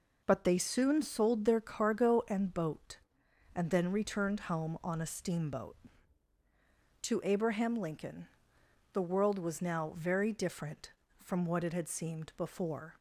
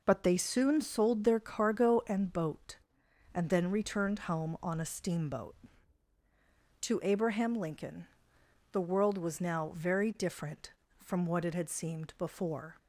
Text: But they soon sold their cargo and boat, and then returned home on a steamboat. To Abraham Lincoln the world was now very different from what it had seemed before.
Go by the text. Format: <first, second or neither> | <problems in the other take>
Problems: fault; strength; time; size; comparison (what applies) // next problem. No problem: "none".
neither | pauses between "Lincoln" and "the"; noticeable; the same in both